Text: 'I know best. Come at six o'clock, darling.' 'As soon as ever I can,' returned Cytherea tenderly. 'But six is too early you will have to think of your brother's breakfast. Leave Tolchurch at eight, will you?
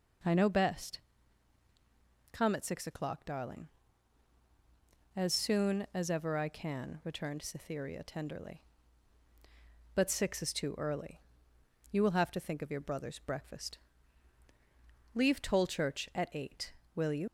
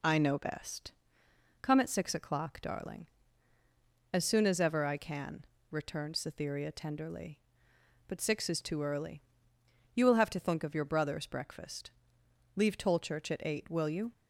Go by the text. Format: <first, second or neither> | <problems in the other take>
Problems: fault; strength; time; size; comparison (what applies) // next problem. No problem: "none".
second | pauses between "early" and "you"; noticeable; at 11.2 s; 0.74 s long; noticeable in the second // leaves "you" unfinished; at 17.2 s; 60 ms